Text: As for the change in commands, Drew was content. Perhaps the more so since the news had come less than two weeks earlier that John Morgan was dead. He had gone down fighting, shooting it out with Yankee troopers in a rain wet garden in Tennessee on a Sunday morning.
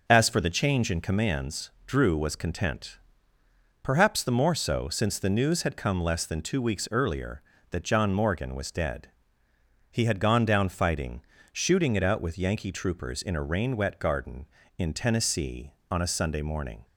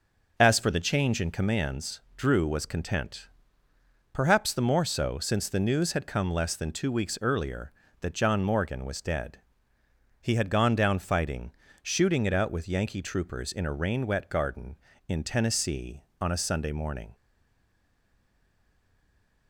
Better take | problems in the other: first | stays silent after the last word; from 17.1 s on; 2.3 s long

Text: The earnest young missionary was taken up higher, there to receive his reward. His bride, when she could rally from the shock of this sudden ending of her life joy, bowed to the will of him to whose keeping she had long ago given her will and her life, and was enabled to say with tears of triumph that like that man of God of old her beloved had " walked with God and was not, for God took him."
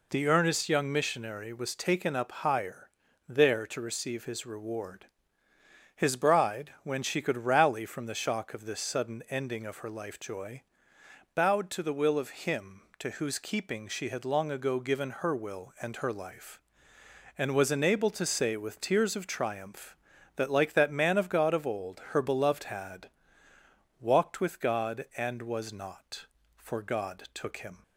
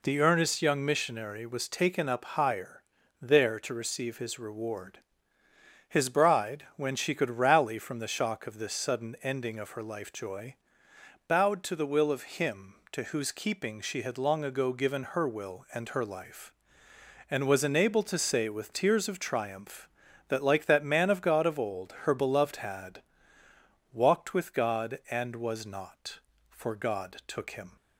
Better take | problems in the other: neither | none

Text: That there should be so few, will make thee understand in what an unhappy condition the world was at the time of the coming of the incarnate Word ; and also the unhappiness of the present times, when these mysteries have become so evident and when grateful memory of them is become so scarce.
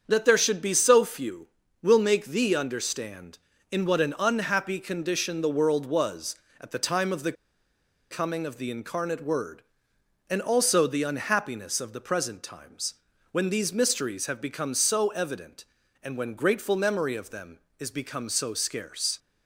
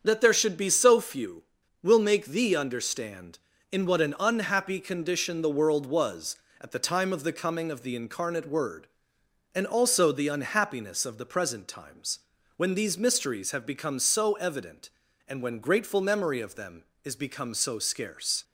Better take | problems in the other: second | starts louder than the rest; strong; until 1.0 s; 7 dB; strong in the second // pauses between "the" and "coming"; noticeable; at 7.3 s; 0.78 s long

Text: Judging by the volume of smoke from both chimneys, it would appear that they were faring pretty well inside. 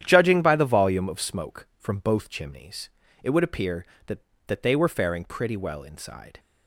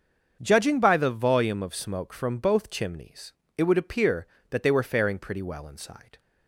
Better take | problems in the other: second | starts louder than the rest; strong; until 1.0 s; 10 dB; also in the second // says "that" twice; at 4.4 s

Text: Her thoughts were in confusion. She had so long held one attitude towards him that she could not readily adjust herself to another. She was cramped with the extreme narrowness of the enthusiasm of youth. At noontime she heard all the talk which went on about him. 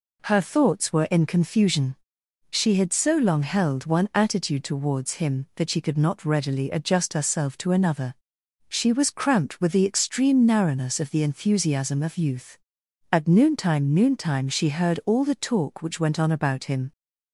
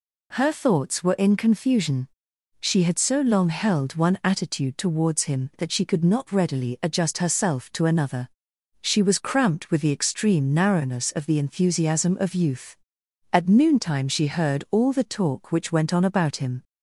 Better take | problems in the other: second | says "noontime" twice; at 13.9 s

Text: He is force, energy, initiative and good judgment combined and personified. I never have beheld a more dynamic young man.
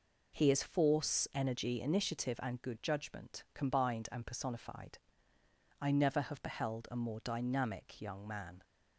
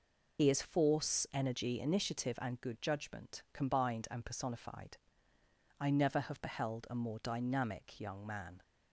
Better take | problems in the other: first | loses the start of "He"; at 0.3 s; 75 ms

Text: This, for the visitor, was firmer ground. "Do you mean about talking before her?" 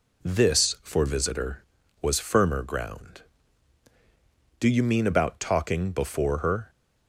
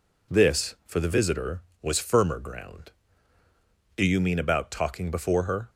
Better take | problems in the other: second | skips "the"; at 1.0 s

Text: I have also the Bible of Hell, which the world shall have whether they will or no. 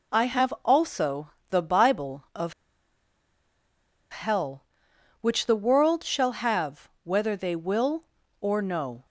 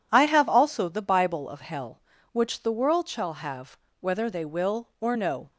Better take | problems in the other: second | pauses between "also" and "the"; slight; at 1.3 s; 0.18 s long // pauses between "of" and "Hell"; strong; at 2.5 s; 1.5 s long // pauses between "have" and "whether"; slight; at 6.8 s; 0.16 s long; slight in the second

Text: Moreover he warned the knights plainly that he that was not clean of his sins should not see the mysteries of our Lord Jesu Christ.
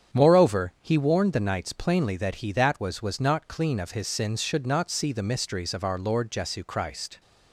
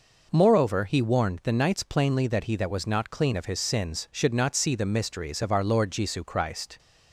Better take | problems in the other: second | starts louder than the rest; strong; until 1.2 s; 8 dB // says "was" twice; at 2.9 s

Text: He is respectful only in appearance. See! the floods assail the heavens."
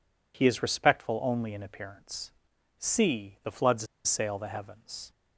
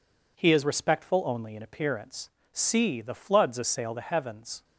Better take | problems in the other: second | pauses between "floods" and "assail"; slight; at 3.8 s; 0.21 s long

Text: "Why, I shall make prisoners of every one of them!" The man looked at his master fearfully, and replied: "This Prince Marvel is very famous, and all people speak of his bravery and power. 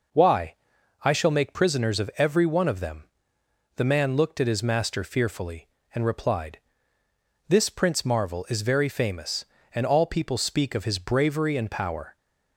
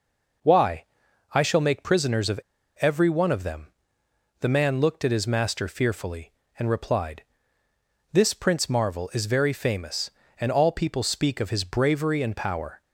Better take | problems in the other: first | pauses between "of" and "every"; at 2.3 s; 0.41 s long

